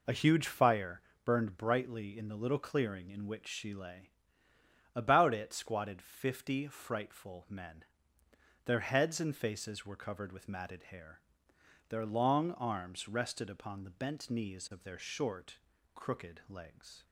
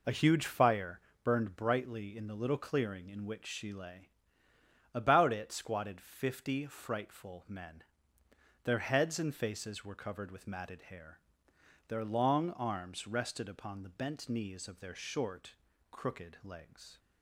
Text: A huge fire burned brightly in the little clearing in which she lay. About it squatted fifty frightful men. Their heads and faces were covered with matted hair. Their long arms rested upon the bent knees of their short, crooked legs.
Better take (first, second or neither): neither